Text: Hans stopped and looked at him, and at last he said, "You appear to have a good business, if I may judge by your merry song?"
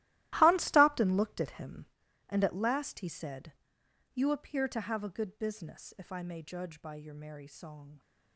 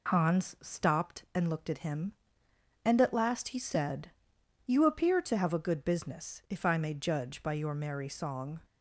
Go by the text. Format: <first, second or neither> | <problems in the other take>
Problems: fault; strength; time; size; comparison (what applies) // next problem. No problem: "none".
second | gets quieter; strong; throughout; 15.5 dB